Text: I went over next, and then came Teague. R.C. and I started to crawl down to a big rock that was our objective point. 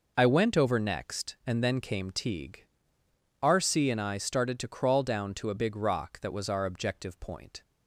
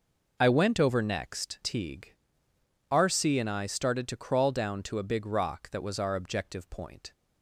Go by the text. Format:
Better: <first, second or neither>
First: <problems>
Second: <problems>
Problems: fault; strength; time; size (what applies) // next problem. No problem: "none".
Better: first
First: none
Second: skips "and then came"; at 1.6 s